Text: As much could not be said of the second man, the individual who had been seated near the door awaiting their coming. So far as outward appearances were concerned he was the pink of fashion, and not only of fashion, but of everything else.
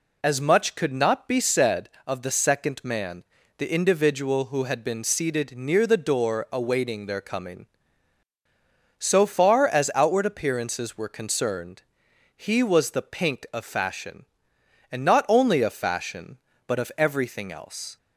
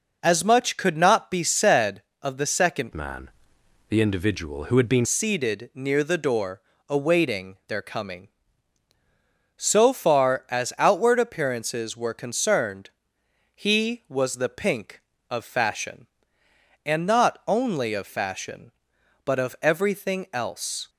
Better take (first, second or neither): first